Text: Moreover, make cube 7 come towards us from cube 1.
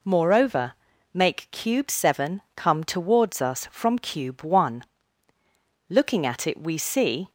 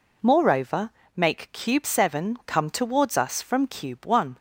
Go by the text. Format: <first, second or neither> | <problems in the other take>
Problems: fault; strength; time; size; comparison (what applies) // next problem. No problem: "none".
second | goes on to say "Looking at it we see"; from 5.8 s on; 1.4 s long